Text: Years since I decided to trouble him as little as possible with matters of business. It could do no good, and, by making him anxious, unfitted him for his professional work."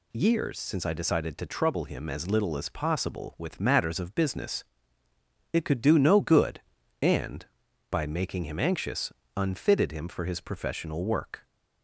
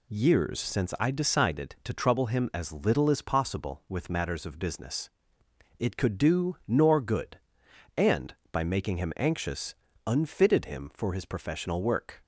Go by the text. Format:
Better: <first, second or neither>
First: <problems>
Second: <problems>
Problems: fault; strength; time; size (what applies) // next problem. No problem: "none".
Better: first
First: none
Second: says "nor" for "no"; at 6.6 s